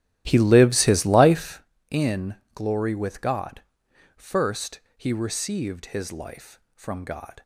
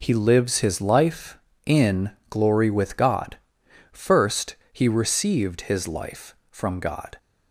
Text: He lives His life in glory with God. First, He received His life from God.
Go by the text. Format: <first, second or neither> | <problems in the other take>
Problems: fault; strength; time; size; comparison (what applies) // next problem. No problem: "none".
second | starts louder than the rest; strong; until 1.7 s; 13 dB // pauses between "in" and "glory"; slight; at 2.3 s; 0.22 s long; slight in the second